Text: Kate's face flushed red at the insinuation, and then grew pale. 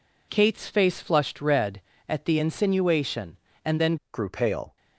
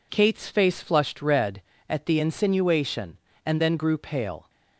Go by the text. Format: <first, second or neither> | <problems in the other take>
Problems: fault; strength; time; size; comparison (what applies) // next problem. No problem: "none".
second | changes voice at "grew"; from 4.1 s on; 0.6 s long